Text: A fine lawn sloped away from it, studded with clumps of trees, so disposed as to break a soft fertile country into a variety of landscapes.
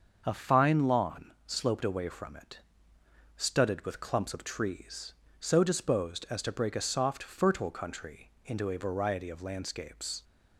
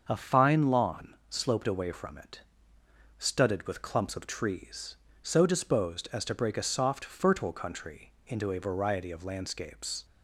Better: neither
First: starts louder than the rest; until 1.2 s; 6.5 dB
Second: starts louder than the rest; until 1.1 s; 6.5 dB

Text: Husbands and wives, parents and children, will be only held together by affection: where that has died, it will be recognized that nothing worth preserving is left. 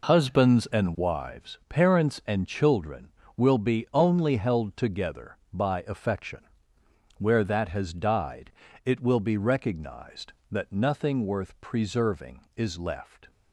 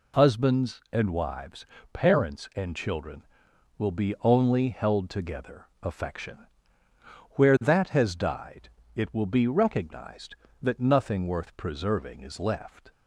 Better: first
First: none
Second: skips "by"; at 5.7 s

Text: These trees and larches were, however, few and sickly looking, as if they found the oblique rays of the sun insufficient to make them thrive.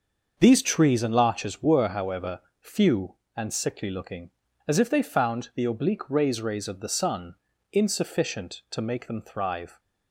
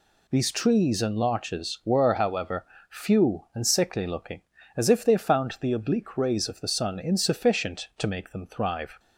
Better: second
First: starts louder than the rest; until 1.4 s; 6.5 dB // says "rays" twice; at 6.4 s // pauses between "sun" and "insufficient"; slight; at 7.3 s; 0.36 s long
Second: none

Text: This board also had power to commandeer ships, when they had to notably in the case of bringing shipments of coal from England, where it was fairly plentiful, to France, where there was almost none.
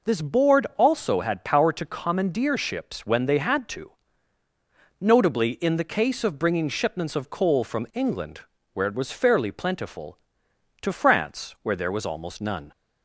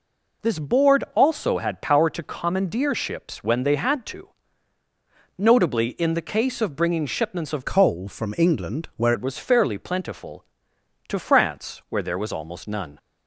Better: first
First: pauses between "to" and "notably"; at 3.9 s; 1.0 s long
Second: pauses between "to" and "notably"; at 4.2 s; 1.0 s long // changes voice from "coal" to "where"; from 7.6 to 9.1 s; 1.5 s long

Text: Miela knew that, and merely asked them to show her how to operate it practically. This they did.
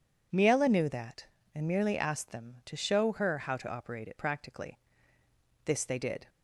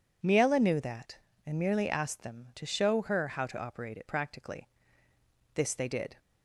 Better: neither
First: none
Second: none

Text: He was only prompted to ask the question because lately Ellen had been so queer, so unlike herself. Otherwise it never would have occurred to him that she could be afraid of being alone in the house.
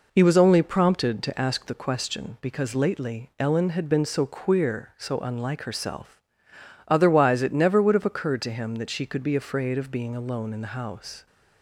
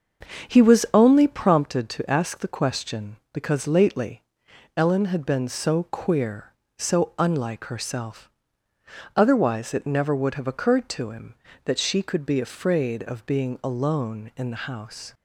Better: first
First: none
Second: starts louder than the rest; strong; until 1.7 s; 7 dB // pauses between "lately" and "Ellen"; noticeable; at 4.2 s; 0.54 s long

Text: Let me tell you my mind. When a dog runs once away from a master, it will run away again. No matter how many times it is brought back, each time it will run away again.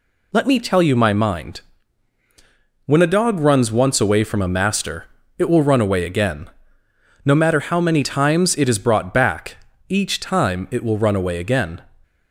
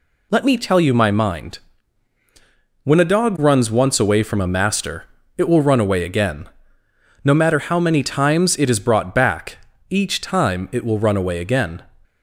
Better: neither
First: none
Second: none

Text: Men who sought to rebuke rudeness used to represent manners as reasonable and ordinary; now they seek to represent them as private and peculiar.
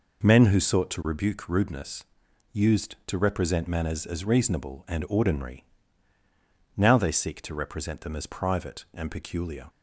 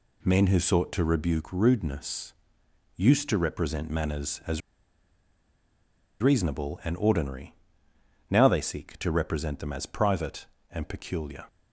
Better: first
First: pauses between "rudeness" and "used"; noticeable; at 2.0 s; 0.48 s long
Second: pauses between "rudeness" and "used"; noticeable; at 2.3 s; 0.64 s long // pauses between "as" and "reasonable"; strong; at 4.6 s; 1.6 s long

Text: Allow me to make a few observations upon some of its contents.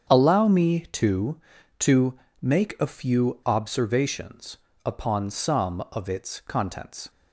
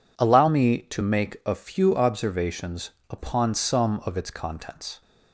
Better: second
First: starts louder than the rest; strong; until 1.1 s; 7.5 dB // says "to" twice; at 1.8 s // pauses between "observations" and "upon"; slight; at 4.5 s; 0.26 s long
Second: pauses between "observations" and "upon"; slight; at 2.9 s; 0.18 s long

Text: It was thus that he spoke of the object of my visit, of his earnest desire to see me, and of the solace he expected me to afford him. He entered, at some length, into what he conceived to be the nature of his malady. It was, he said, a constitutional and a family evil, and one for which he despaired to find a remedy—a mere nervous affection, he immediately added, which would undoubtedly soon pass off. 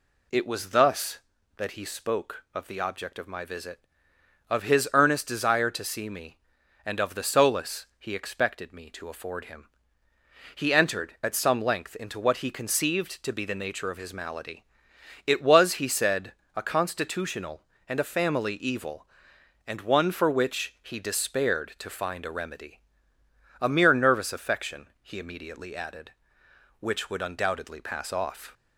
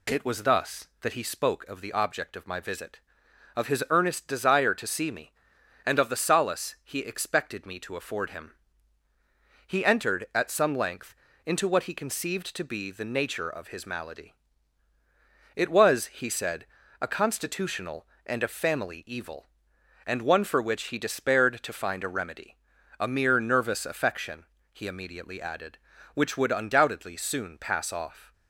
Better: second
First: skips "soon"; at 27.7 s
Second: none

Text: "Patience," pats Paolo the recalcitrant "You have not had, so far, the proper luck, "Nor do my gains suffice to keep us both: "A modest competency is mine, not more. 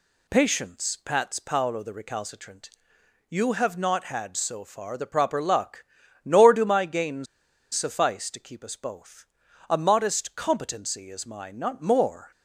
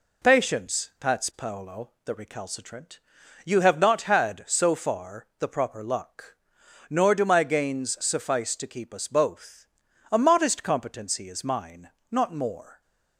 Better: second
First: pauses between "recalcitrant" and "You"; noticeable; at 2.6 s; 0.60 s long // pauses between "gains" and "suffice"; noticeable; at 7.2 s; 0.48 s long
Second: pauses between "recalcitrant" and "You"; noticeable; at 2.9 s; 0.46 s long

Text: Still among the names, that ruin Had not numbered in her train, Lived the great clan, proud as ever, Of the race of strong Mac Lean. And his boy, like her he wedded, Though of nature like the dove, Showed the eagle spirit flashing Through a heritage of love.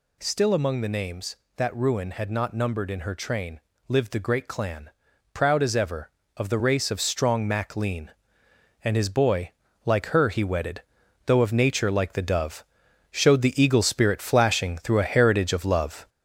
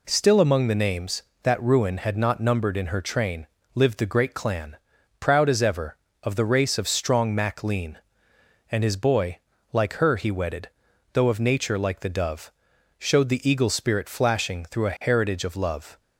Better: second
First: gets louder; noticeable; throughout; 5 dB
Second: none

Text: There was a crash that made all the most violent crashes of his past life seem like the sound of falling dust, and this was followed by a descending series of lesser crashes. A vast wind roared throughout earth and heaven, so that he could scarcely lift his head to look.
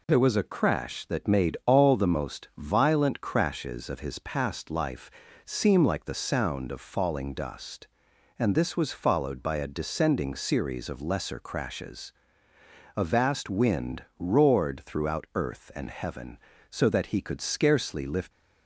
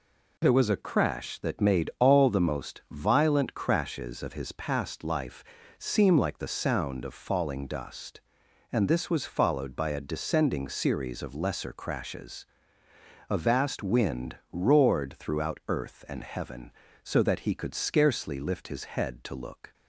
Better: second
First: pauses between "life" and "seem"; slight; at 5.0 s; 0.36 s long // stops before "his head to look"; at 18.3 s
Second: pauses between "life" and "seem"; slight; at 5.4 s; 0.36 s long

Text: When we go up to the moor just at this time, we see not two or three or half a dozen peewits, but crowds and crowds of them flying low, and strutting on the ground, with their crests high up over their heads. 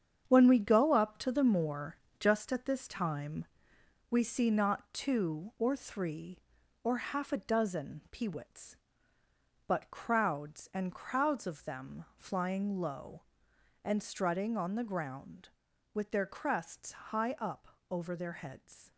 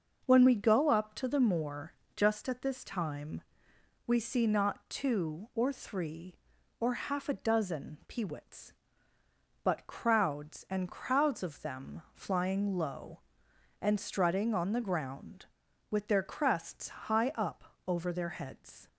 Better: second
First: gets quieter; strong; throughout; 8.5 dB // starts louder than the rest; strong; until 1.2 s; 8 dB // pauses between "moor" and "just"; slight; at 1.9 s; 0.22 s long // pauses between "up" and "over"; slight; at 17.6 s; 0.24 s long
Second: starts louder than the rest; noticeable; until 1.2 s; 6 dB // pauses between "moor" and "just"; slight; at 1.9 s; 0.22 s long // pauses between "up" and "over"; slight; at 17.6 s; 0.24 s long

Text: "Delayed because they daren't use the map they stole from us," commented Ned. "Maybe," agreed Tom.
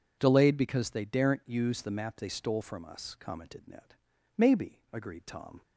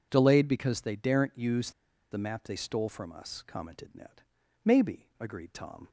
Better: first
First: none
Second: pauses between "use" and "the"; at 1.7 s; 0.41 s long

